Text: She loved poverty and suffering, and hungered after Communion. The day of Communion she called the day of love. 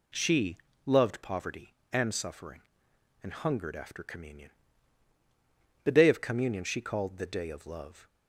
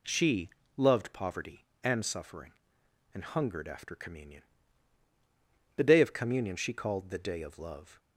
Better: neither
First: pauses between "She" and "loved"; slight; at 0.5 s; 0.26 s long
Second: pauses between "She" and "loved"; slight; at 0.5 s; 0.24 s long

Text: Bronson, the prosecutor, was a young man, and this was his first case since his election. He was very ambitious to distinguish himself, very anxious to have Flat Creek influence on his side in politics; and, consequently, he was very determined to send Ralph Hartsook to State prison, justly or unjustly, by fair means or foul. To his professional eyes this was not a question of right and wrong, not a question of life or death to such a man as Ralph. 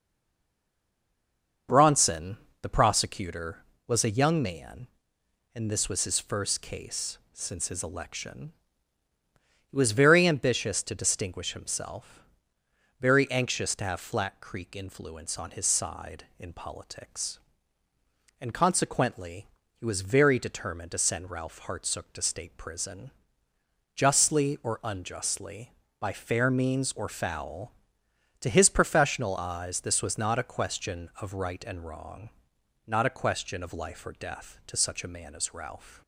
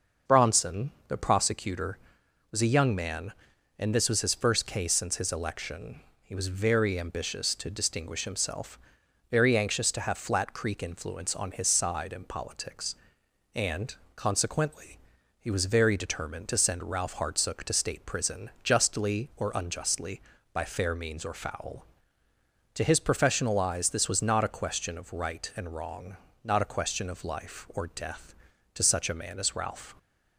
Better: second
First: stays silent before the first word; noticeable; until 1.6 s; 1.6 s long // starts louder than the rest; until 2.9 s; 6.5 dB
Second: starts louder than the rest; noticeable; until 1.4 s; 6 dB

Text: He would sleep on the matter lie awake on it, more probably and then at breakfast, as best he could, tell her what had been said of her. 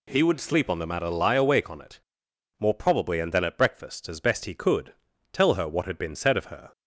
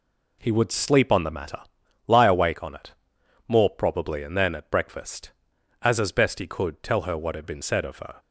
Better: first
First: none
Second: pauses between "matter" and "lie"; noticeable; at 1.5 s; 0.48 s long // says "as" twice; at 5.9 s

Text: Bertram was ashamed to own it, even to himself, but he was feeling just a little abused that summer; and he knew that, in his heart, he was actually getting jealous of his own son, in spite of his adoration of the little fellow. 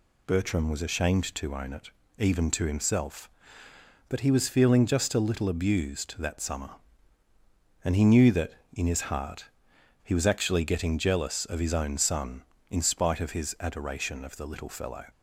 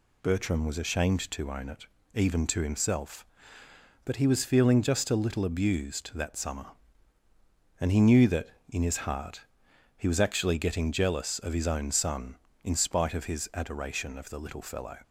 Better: neither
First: none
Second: none

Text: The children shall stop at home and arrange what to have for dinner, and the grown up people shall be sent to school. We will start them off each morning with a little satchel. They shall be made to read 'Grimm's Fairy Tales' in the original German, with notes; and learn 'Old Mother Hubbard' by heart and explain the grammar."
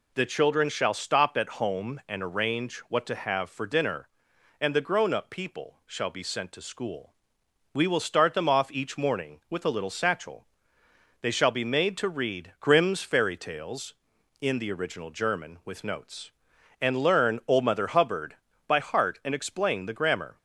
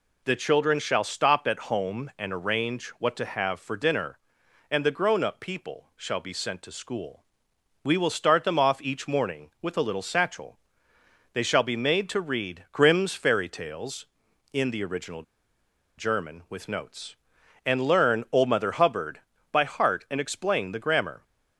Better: first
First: none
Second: pauses between "original" and "German"; noticeable; at 15.2 s; 0.74 s long

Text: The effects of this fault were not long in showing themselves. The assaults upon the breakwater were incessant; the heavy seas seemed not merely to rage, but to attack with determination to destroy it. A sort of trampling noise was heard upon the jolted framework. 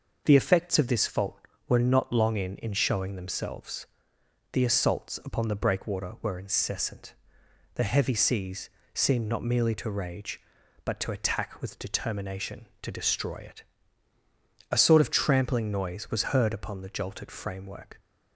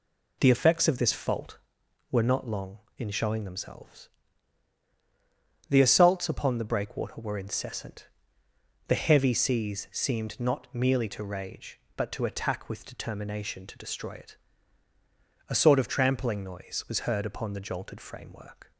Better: second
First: says "in" twice; at 2.5 s // pauses between "seas" and "seemed"; slight; at 8.6 s; 0.24 s long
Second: none

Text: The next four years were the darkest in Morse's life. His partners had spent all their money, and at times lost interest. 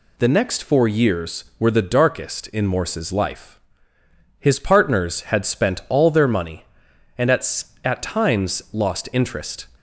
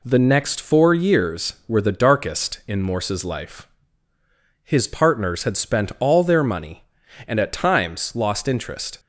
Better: second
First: says "at" twice; at 7.8 s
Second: none

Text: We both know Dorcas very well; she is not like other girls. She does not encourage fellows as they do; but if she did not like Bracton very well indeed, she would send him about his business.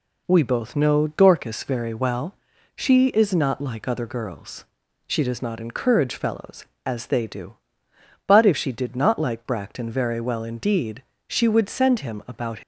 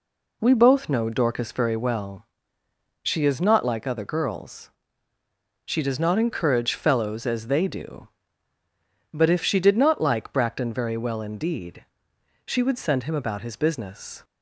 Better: second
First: stops before "his business"; at 12.6 s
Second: none

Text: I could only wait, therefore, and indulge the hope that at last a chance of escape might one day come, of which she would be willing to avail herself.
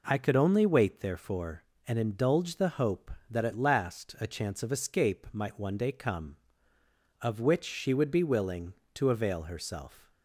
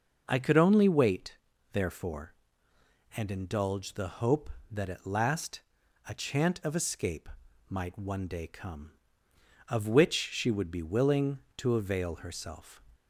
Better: first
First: none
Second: pauses between "last" and "a"; noticeable; at 5.6 s; 0.48 s long // says "chant" for "chance"; at 6.1 s // pauses between "escape" and "might"; at 7.2 s; 0.40 s long

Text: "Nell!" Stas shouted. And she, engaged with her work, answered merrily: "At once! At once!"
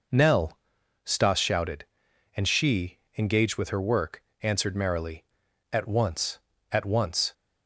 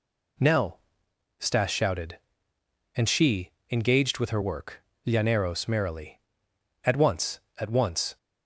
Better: first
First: none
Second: says "llaneros" for "answered"; at 5.0 s

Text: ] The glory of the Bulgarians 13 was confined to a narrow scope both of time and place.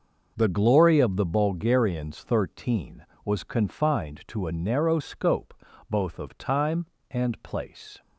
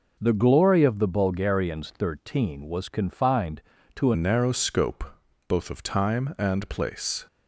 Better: first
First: pauses between "scope" and "both"; at 5.5 s; 0.38 s long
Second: changes voice at "narrow"; from 4.1 s on; 3.1 s long // pauses between "scope" and "both"; noticeable; at 5.0 s; 0.46 s long

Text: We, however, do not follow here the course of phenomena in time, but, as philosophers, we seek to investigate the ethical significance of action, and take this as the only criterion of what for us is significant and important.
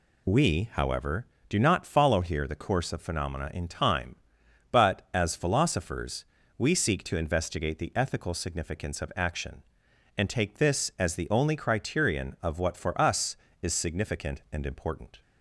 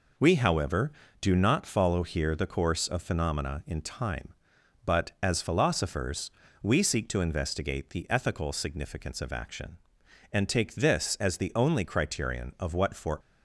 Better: first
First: none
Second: stops before "us is significant and important"; at 13.2 s

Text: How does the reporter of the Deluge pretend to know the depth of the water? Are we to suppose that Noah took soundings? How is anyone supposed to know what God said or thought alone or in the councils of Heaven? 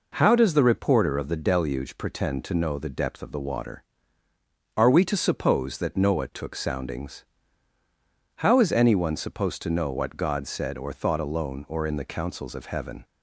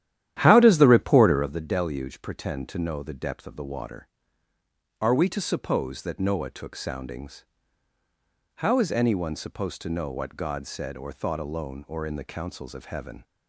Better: first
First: none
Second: starts louder than the rest; strong; until 1.5 s; 11.5 dB

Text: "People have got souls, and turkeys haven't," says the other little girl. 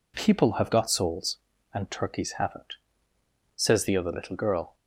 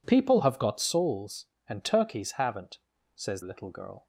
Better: first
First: none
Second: skips "the other"; at 3.4 s

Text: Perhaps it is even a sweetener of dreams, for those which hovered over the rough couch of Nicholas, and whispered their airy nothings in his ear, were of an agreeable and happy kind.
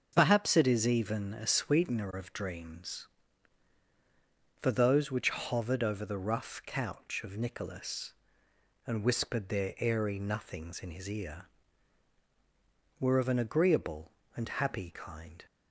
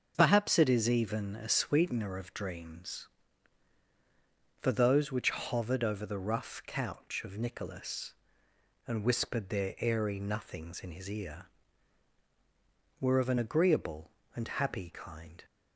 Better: neither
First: starts louder than the rest; until 1.1 s; 6.5 dB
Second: starts louder than the rest; until 1.1 s; 6.5 dB

